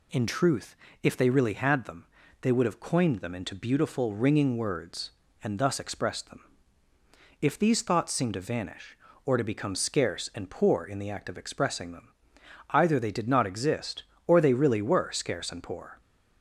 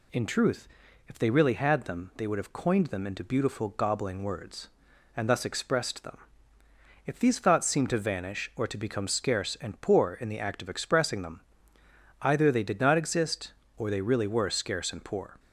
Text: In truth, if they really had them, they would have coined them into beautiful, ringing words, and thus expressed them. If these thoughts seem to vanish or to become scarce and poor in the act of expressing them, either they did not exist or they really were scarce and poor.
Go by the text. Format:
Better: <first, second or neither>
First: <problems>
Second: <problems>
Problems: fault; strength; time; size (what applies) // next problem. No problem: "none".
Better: first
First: none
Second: says "gobbling" for "ringing"; at 3.6 s